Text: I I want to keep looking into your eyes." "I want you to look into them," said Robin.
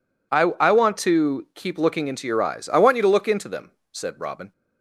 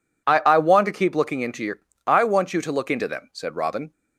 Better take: first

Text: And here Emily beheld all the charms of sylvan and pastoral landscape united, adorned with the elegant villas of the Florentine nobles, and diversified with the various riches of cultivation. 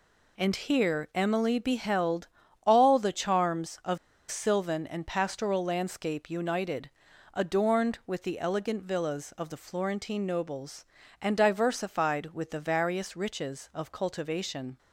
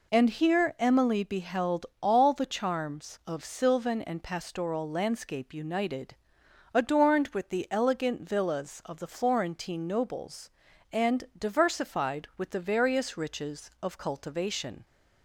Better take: second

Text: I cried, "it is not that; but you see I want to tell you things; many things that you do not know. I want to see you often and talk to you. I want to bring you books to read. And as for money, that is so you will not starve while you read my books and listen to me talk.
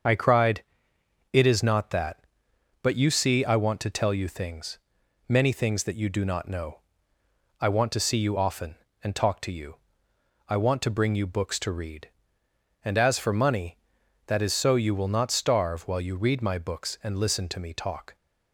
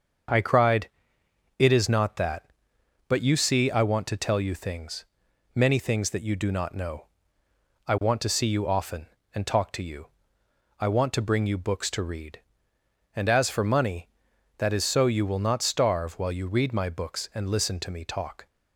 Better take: second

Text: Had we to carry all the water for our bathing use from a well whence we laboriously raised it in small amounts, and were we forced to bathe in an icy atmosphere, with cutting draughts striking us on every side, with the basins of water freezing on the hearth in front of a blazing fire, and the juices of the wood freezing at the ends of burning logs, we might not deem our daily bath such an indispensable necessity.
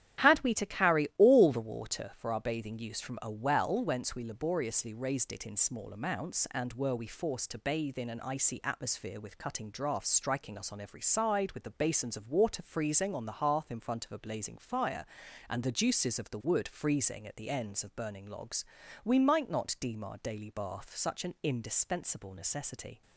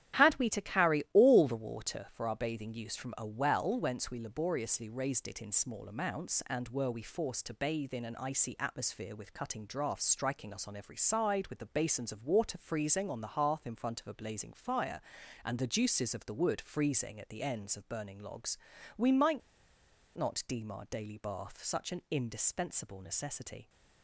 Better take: first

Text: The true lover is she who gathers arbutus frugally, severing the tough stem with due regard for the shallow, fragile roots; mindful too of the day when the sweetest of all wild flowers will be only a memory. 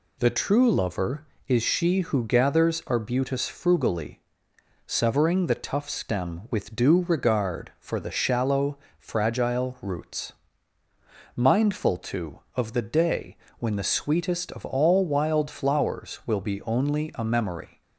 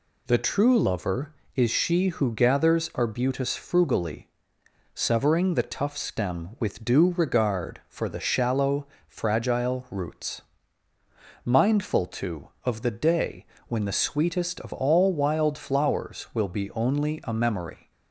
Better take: neither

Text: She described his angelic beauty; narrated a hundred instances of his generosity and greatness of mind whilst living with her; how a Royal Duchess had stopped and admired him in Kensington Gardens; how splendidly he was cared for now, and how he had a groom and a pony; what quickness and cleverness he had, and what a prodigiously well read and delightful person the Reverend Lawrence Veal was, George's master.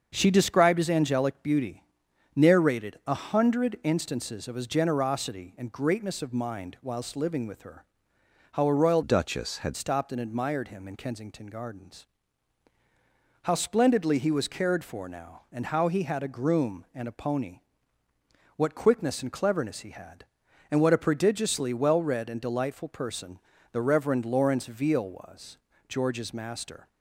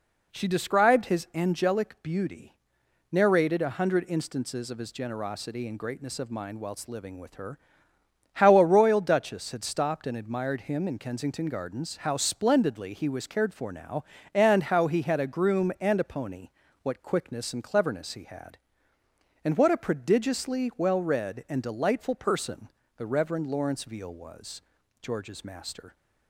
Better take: second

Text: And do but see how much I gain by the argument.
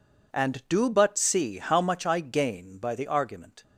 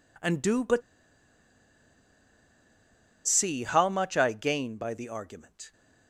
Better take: first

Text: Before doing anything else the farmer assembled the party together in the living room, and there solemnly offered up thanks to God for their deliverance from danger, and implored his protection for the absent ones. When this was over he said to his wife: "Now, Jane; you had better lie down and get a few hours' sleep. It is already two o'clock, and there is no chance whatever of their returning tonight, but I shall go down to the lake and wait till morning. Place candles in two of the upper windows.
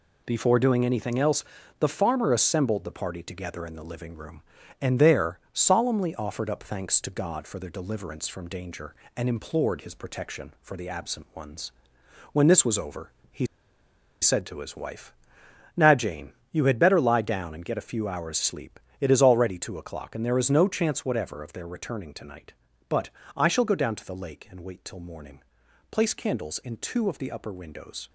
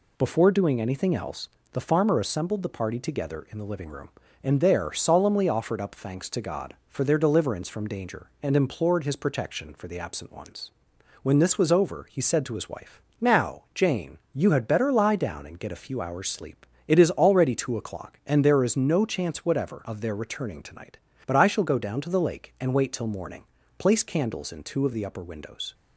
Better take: second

